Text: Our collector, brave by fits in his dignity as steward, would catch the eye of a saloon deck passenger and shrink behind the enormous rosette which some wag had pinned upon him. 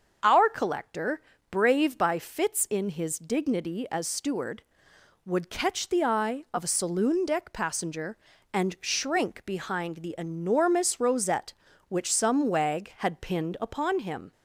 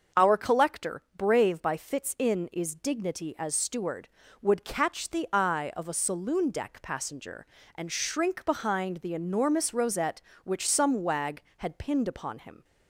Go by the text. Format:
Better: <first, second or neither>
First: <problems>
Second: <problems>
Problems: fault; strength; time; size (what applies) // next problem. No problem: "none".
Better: first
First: starts louder than the rest; until 1.5 s; 6.5 dB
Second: starts louder than the rest; until 1.3 s; 6.5 dB // says "is" for "his"; at 2.5 s